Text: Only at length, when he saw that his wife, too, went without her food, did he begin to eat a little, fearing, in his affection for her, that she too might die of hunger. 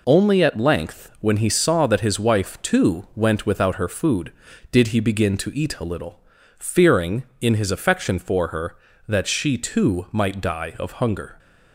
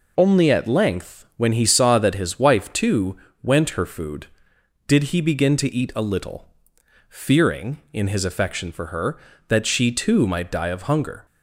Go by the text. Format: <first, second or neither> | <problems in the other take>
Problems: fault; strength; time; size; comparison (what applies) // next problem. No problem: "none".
first | skips "without"; at 3.7 s